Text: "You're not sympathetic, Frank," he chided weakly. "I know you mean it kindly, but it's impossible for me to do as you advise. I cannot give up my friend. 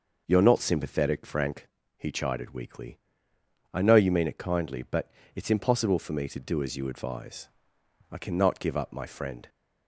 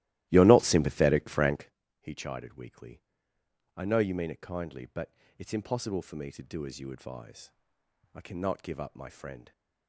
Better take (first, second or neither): first